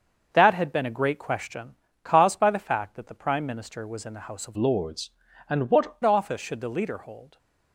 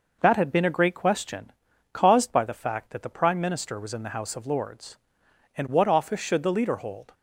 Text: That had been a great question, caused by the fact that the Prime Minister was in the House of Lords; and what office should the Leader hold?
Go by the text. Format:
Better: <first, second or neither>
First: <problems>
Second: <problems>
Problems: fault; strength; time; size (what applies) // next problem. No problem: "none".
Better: second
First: starts louder than the rest; until 1.3 s; 6.5 dB // changes voice from "Lords" to "what"; from 4.5 to 5.9 s; 1.4 s long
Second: none